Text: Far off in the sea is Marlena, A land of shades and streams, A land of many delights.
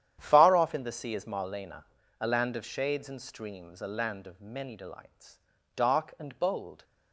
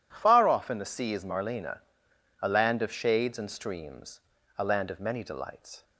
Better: second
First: starts louder than the rest; strong; until 1.2 s; 10 dB // goes on to say "Dark and bold"; noticeable; from 5.7 s on; 1.0 s long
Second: none

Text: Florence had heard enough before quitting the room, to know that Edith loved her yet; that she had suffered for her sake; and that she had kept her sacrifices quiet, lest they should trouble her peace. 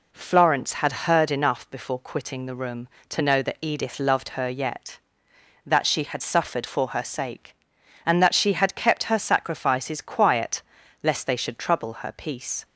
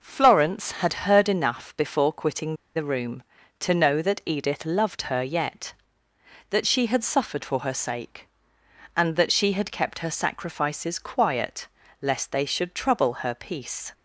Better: first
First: none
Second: pauses between "quitting" and "the"; slight; at 2.5 s; 0.19 s long

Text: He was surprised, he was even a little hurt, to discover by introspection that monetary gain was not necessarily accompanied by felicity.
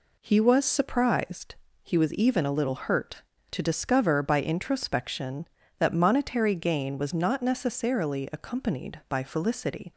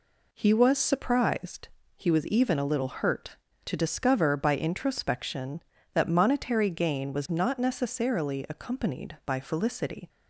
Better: neither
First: none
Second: none

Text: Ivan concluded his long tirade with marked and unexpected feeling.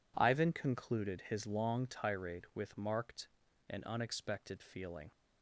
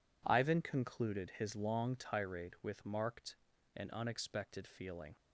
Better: neither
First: none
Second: none

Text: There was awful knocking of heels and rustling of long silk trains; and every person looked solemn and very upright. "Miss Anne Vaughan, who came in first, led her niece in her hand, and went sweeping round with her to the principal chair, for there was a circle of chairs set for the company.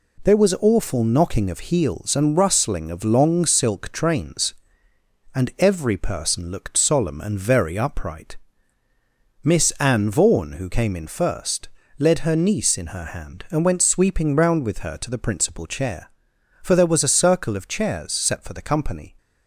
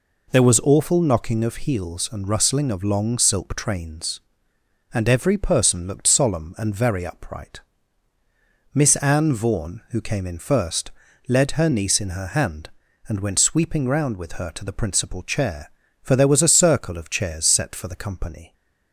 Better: neither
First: none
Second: none

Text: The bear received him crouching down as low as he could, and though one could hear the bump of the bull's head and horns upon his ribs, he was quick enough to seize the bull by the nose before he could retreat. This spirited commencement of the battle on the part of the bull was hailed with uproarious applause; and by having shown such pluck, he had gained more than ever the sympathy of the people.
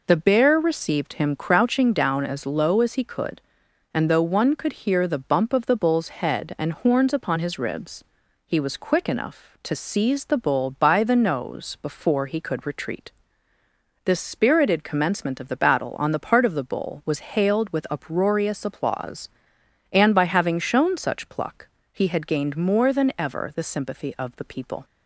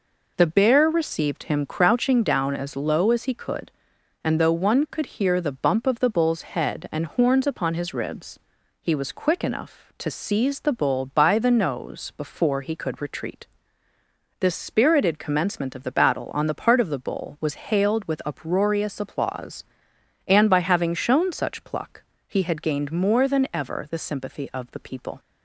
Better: neither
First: none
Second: none

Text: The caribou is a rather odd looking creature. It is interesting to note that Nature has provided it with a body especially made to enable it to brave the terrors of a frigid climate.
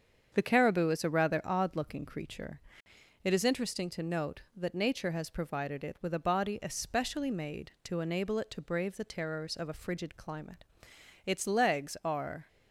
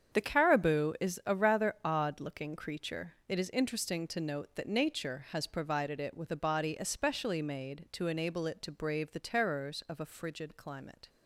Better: second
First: starts louder than the rest; strong; until 1.3 s; 7.5 dB // goes on to say "Its legs are"; noticeable; from 11.2 s on; 1.2 s long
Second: starts louder than the rest; strong; until 1.2 s; 7.5 dB

